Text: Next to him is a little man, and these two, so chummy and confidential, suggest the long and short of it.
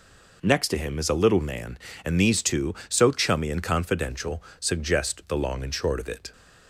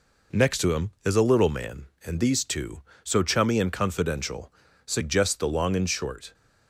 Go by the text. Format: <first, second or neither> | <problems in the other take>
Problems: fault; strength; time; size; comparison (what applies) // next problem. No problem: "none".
first | stops before "of it"; at 6.3 s